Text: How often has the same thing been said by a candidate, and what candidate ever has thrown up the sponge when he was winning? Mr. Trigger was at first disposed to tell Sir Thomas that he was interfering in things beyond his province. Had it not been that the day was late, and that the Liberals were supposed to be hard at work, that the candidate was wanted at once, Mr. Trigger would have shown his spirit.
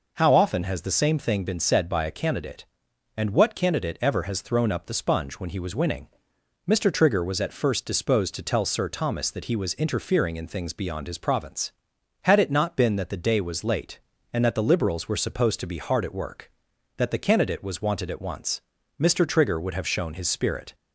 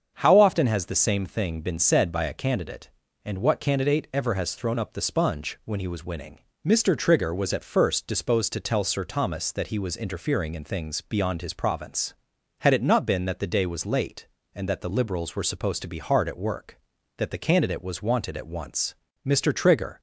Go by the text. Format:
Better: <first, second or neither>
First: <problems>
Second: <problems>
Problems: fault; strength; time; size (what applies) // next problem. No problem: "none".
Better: first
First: none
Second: starts louder than the rest; until 1.1 s; 7 dB // stops before "would have shown his spirit"; at 19.9 s